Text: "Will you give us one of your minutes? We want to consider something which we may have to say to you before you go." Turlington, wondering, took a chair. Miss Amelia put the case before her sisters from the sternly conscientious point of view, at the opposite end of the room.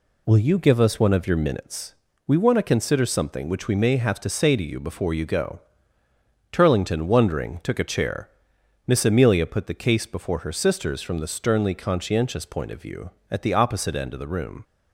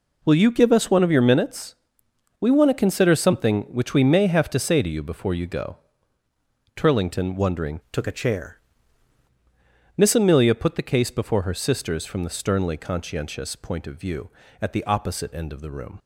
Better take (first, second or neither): first